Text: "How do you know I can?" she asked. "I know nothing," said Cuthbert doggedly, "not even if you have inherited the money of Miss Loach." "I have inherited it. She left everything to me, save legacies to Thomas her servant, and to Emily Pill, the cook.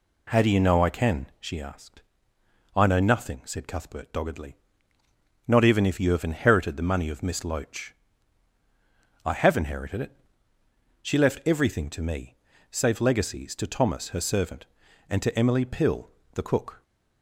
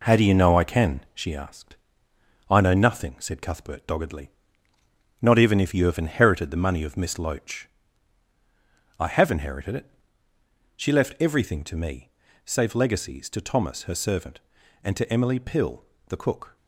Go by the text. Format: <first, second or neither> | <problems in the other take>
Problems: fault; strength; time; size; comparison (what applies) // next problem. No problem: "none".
first | gets quieter; noticeable; throughout; 5.5 dB